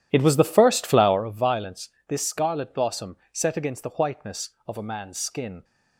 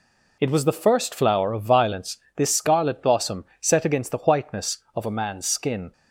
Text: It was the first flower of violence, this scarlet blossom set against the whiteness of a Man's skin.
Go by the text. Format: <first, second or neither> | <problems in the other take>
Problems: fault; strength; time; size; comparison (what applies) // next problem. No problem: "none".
second | starts louder than the rest; strong; until 1.2 s; 11.5 dB // pauses between "blossom" and "set"; slight; at 3.1 s; 0.16 s long; slight in the second